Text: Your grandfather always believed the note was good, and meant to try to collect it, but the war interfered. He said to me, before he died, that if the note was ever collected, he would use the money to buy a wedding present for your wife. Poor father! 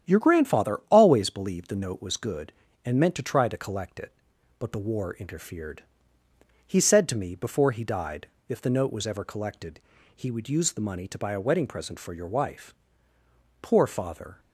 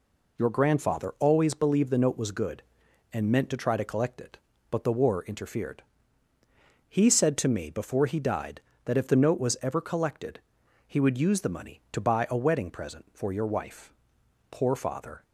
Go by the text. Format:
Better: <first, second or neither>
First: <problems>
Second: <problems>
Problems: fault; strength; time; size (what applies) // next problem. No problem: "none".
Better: second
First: starts louder than the rest; strong; until 1.1 s; 9.5 dB // skips "that"; at 8.3 s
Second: none